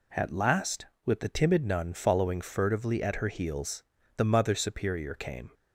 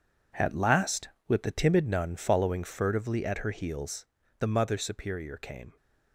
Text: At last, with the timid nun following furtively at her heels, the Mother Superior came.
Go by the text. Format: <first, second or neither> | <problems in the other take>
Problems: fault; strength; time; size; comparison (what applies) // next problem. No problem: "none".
first | gets quieter; strong; throughout; 11 dB